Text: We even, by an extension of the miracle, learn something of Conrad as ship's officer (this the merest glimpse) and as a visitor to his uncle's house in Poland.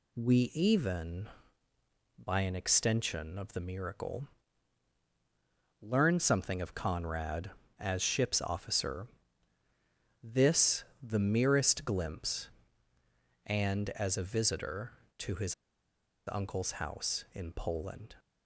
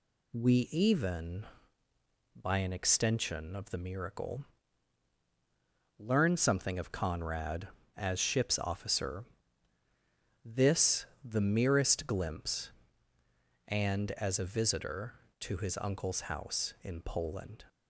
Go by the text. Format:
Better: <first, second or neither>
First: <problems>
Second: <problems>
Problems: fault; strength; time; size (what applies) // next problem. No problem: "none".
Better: second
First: pauses between "this" and "the"; slight; at 10.8 s; 0.18 s long // pauses between "his" and "uncle's"; noticeable; at 15.5 s; 0.73 s long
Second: pauses between "this" and "the"; slight; at 11.0 s; 0.18 s long